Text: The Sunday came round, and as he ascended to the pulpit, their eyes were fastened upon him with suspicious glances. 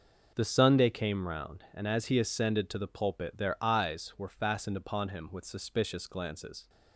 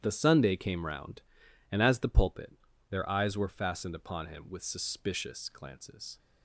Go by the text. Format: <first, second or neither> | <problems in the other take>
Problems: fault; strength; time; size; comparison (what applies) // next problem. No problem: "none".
first | starts louder than the rest; strong; until 1.0 s; 10 dB // skips "he ascended to"; at 1.9 s